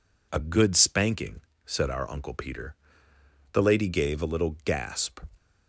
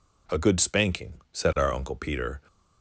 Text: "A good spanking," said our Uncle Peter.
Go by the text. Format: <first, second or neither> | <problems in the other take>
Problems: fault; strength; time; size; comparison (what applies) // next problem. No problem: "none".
second | goes on to say "The Lady gave a little gasp"; from 3.5 s on; 1.6 s long